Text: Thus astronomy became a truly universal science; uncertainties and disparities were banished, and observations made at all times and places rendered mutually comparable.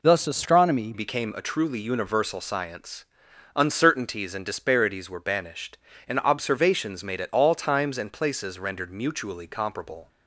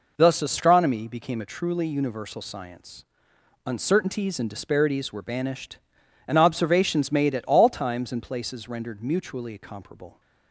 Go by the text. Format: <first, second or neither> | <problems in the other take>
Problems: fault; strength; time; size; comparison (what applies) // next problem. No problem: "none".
second | changes voice at "became"; from 0.9 s on; 9.1 s long